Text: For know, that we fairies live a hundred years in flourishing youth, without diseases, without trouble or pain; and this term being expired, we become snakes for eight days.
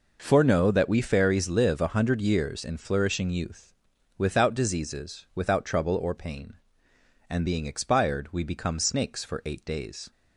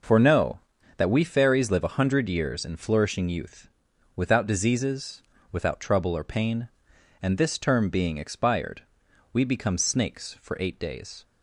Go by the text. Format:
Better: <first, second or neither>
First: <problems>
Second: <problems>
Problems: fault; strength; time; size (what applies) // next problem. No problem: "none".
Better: second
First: skips "this term"; at 7.4 s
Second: none